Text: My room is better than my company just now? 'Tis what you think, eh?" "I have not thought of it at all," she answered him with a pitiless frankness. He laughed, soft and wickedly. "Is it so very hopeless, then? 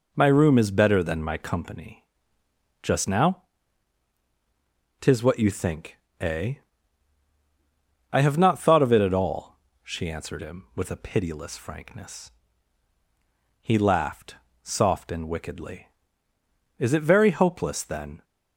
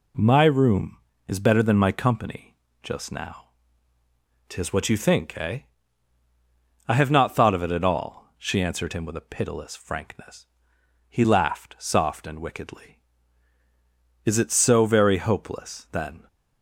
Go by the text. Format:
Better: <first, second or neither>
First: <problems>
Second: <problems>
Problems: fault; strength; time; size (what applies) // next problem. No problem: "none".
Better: second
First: pauses between "company" and "just"; noticeable; at 2.0 s; 0.78 s long // skips "so"; at 17.1 s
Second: pauses between "company" and "just"; slight; at 2.5 s; 0.26 s long